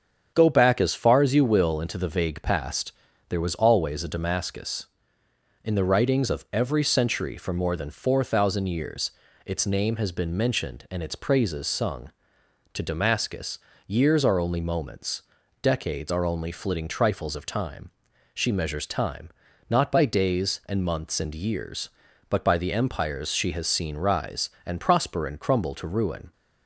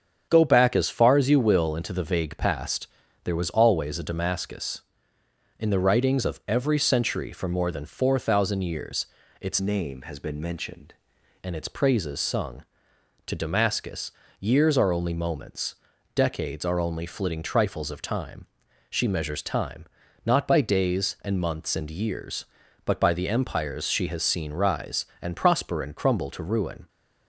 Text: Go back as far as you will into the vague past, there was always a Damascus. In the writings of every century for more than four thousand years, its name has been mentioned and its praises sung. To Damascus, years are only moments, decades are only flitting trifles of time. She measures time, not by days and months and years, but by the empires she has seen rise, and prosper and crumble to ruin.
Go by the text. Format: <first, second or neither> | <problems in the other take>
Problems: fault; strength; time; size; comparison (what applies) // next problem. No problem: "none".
first | starts louder than the rest; strong; until 1.3 s; 7.5 dB; strong in the first // changes voice from "name" to "mentioned"; from 9.6 to 10.9 s; 1.3 s long